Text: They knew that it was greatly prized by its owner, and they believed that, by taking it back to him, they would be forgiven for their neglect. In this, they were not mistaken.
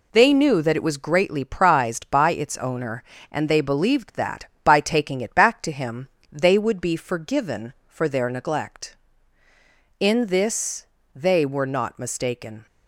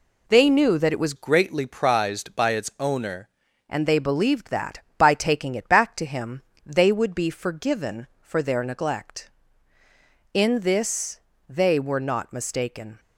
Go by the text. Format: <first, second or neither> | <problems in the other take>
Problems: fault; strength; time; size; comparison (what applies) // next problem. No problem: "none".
first | changes voice from "greatly" to "owner"; from 1.1 to 3.2 s; 2.1 s long